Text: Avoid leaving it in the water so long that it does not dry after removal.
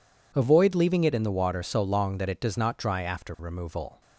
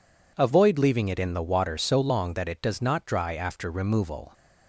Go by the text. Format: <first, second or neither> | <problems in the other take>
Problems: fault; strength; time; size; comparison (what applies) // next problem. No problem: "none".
neither | none